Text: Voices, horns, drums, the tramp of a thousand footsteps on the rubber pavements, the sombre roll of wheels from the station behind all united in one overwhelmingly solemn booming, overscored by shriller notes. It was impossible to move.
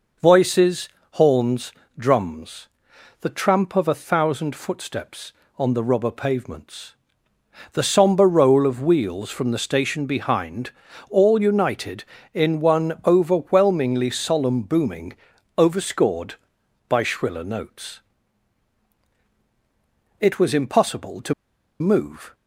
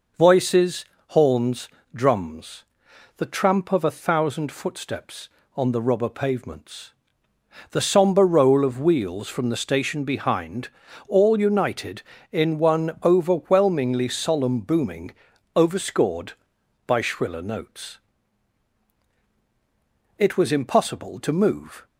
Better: second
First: pauses between "behind" and "all"; at 10.7 s; 0.38 s long // pauses between "to" and "move"; noticeable; at 21.3 s; 0.46 s long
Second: pauses between "behind" and "all"; at 10.6 s; 0.38 s long

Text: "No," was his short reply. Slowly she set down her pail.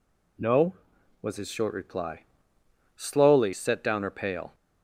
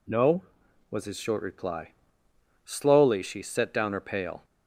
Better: second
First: skips "she"; at 3.5 s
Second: none

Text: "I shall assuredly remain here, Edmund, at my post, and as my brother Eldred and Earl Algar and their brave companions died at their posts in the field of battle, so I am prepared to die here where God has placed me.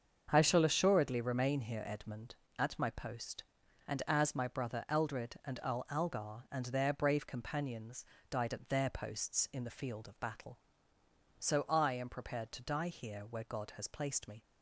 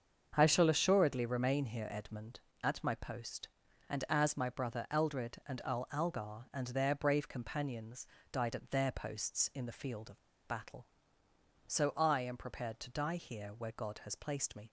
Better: first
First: starts louder than the rest; until 1.3 s; 7 dB // pauses between "companions" and "died"; slight; at 8.0 s; 0.24 s long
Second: starts louder than the rest; until 1.3 s; 7 dB // pauses between "companions" and "died"; slight; at 8.0 s; 0.24 s long // pauses between "of" and "battle"; slight; at 10.1 s; 0.28 s long

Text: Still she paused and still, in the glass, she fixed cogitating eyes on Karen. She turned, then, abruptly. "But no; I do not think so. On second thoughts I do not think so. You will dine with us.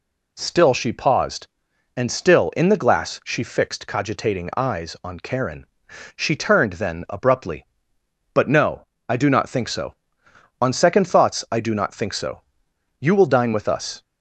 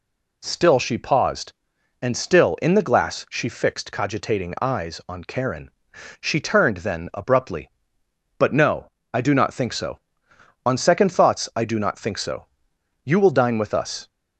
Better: neither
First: none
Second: none

